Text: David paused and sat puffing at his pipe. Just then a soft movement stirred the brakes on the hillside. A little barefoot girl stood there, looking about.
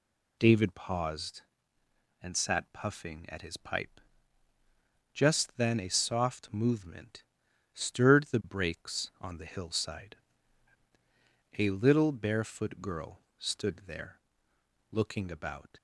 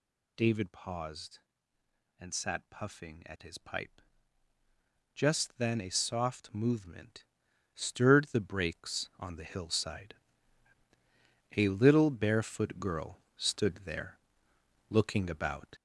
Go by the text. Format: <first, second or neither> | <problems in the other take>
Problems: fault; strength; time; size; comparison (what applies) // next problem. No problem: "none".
first | gets louder; strong; throughout; 8 dB // pauses between "movement" and "stirred"; noticeable; at 7.2 s; 0.50 s long; noticeable in the first // pauses between "girl" and "stood"; slight; at 13.1 s; 0.20 s long; slight in the first